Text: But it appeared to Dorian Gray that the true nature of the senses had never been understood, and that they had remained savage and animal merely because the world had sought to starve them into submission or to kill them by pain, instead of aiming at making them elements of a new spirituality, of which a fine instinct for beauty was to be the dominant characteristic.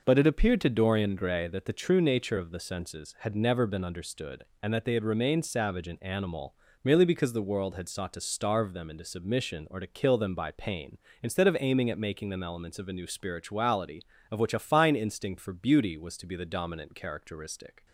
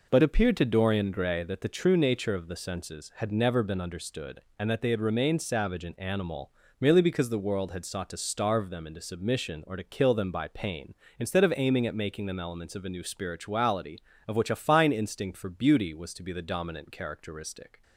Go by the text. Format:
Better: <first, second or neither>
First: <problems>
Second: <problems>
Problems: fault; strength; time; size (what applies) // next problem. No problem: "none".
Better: first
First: pauses between "animal" and "merely"; slight; at 6.5 s; 0.30 s long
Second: skips "it"; at 0.2 s // pauses between "animal" and "merely"; slight; at 6.5 s; 0.30 s long